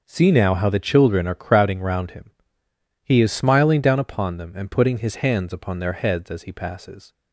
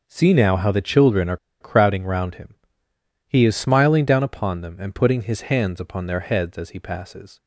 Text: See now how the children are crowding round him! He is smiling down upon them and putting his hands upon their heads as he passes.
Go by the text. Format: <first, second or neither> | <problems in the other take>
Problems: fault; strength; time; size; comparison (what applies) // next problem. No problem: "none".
first | pauses between "are" and "crowding"; slight; at 1.3 s; 0.24 s long